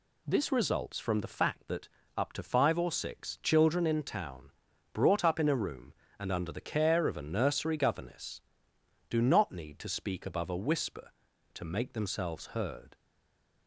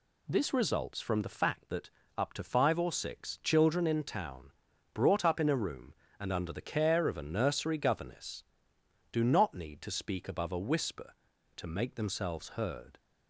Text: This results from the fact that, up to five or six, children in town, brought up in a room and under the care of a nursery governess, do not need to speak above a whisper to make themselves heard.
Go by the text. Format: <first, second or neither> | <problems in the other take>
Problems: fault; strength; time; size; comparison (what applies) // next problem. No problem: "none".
second | stays silent after the last word; slight; from 12.9 s on; 0.7 s long